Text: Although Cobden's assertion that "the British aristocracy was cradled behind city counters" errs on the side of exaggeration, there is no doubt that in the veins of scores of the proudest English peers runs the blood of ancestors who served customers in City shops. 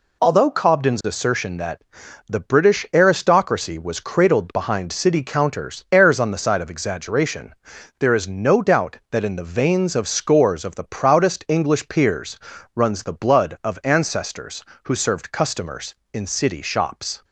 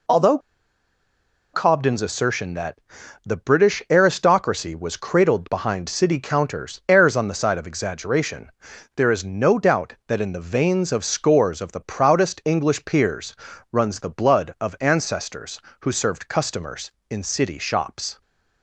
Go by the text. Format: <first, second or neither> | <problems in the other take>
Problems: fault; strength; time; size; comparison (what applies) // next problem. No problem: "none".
first | pauses between "Although" and "Cobden's"; at 0.3 s; 1.1 s long // pauses between "that" and "the"; noticeable; at 2.7 s; 0.46 s long; noticeable in the first // pauses between "peers" and "runs"; at 13.3 s; 0.38 s long; also in the first